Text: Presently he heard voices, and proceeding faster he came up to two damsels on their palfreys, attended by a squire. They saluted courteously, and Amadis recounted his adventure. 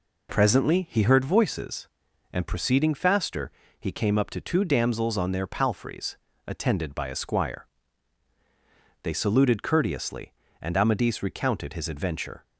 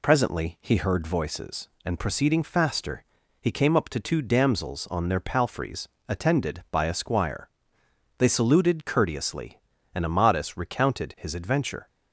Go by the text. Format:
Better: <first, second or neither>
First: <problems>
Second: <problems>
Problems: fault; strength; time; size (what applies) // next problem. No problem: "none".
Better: neither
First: pauses between "faster" and "he"; slight; at 3.5 s; 0.28 s long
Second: pauses between "faster" and "he"; slight; at 3.0 s; 0.34 s long